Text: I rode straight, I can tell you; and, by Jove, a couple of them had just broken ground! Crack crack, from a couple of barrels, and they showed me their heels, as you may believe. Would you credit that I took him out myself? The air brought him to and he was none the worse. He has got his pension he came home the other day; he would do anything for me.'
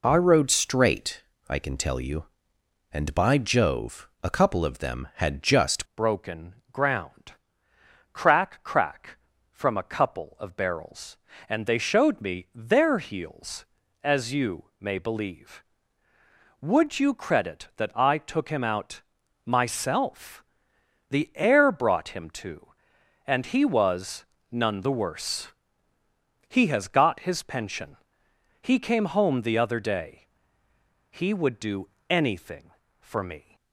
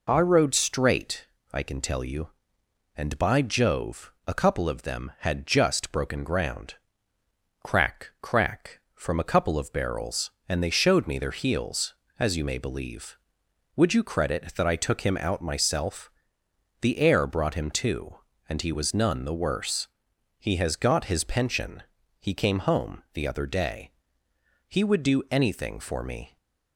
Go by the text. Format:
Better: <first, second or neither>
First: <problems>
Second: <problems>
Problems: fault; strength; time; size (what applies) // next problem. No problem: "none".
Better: second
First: changes voice at "broken"; from 5.9 s on; 27.6 s long // pauses between "broken" and "ground"; slight; at 6.5 s; 0.16 s long // pauses between "out" and "myself"; at 19.0 s; 0.44 s long // pauses between "was" and "none"; slight; at 24.2 s; 0.26 s long // pauses between "pension" and "he"; noticeable; at 27.9 s; 0.64 s long // pauses between "do" and "anything"; slight; at 31.8 s; 0.20 s long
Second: pauses between "pension" and "he"; at 21.8 s; 0.38 s long